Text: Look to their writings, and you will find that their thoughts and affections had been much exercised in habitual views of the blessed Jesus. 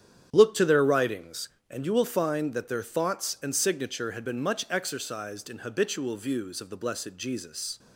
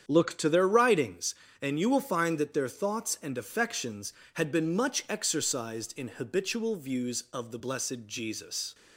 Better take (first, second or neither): second